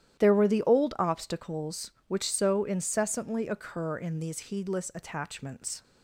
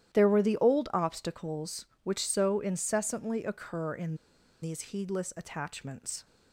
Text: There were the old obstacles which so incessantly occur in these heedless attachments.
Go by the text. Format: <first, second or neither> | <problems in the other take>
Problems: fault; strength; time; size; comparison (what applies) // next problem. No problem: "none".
first | starts louder than the rest; strong; until 1.1 s; 11.5 dB; strong in the first // pauses between "in" and "these"; noticeable; at 4.1 s; 0.46 s long